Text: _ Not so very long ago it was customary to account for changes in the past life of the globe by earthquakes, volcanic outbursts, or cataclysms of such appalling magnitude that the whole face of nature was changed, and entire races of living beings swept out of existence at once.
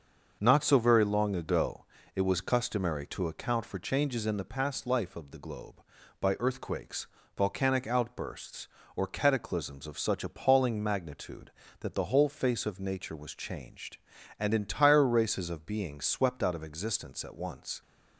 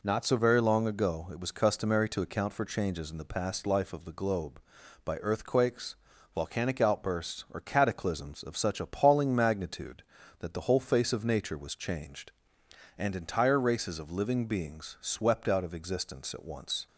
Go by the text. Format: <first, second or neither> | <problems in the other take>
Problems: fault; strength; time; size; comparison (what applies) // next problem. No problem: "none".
second | starts louder than the rest; until 1.4 s; 6 dB // pauses between "ago" and "it"; slight; at 1.8 s; 0.28 s long // skips "living"; at 15.6 s